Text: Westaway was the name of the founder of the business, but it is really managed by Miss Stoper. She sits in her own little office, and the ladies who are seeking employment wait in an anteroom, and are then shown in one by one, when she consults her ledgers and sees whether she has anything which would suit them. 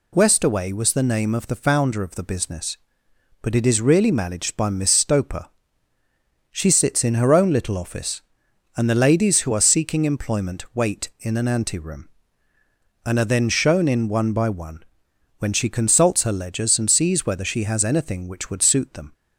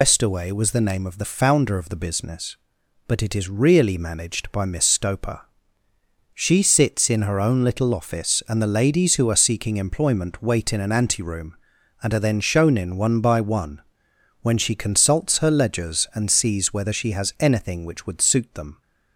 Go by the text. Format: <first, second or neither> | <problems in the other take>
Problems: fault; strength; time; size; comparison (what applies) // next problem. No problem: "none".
first | loses the start of "Westaway"; at 0.0 s; 130 ms